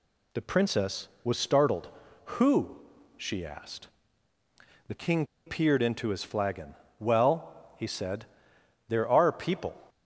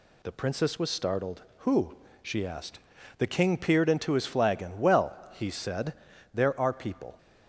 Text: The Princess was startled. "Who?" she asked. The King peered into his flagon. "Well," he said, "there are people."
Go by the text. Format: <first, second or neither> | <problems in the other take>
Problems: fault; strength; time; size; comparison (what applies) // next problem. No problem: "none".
second | pauses between "King" and "peered"; slight; at 5.2 s; 0.21 s long